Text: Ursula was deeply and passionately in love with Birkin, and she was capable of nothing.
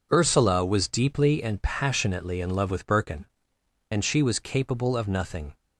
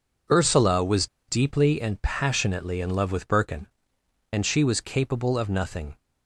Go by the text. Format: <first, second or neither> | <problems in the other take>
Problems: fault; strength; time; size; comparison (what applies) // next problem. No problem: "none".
first | pauses between "was" and "deeply"; slight; at 1.0 s; 0.22 s long